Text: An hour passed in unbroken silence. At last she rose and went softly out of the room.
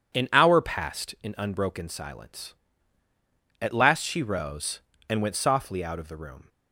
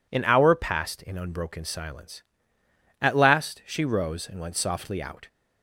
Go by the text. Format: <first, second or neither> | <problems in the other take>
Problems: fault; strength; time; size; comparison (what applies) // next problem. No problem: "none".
first | stops before "of the room"; at 5.2 s